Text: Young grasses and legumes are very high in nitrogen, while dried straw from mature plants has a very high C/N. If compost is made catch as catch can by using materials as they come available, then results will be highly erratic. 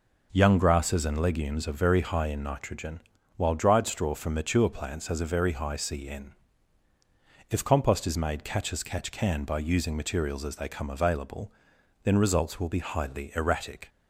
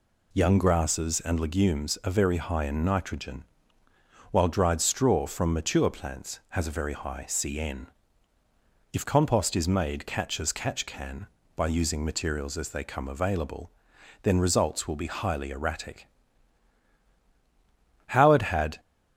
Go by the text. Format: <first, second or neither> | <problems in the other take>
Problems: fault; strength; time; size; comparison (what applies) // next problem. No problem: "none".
first | goes on to say "Howard had"; noticeable; from 18.0 s on; 0.74 s long